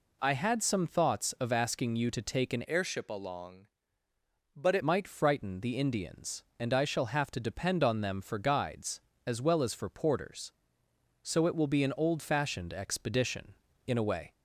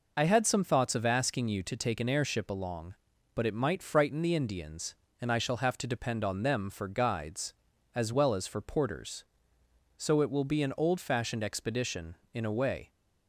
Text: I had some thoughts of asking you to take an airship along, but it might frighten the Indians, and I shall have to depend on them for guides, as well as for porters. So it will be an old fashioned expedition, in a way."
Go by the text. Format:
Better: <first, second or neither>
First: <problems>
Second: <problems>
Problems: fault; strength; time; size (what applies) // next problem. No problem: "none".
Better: second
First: changes voice from "airship" to "it"; from 2.6 to 4.8 s; 2.2 s long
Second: none